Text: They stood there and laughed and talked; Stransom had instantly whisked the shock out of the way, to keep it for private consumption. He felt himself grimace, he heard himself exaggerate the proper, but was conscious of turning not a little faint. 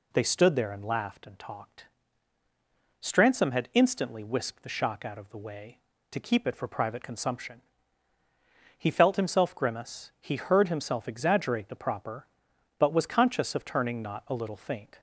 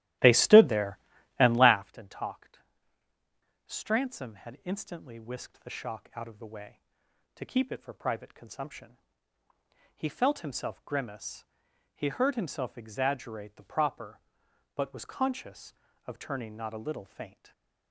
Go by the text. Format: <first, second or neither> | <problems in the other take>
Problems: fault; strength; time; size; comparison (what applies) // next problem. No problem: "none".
first | starts louder than the rest; strong; until 1.8 s; 14 dB // stays silent after the last word; slight; from 17.2 s on; 0.7 s long